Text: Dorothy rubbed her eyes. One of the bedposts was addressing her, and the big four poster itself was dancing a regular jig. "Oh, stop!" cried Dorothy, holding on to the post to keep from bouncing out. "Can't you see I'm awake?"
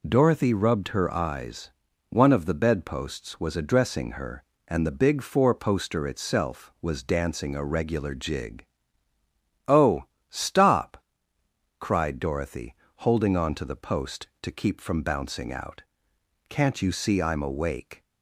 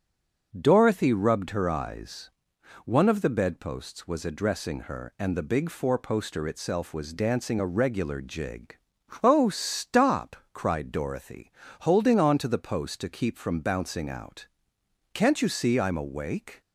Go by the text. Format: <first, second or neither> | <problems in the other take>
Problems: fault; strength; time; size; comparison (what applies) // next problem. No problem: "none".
first | stays silent before the first word; slight; until 0.5 s; 0.5 s long // starts louder than the rest; until 1.5 s; 6 dB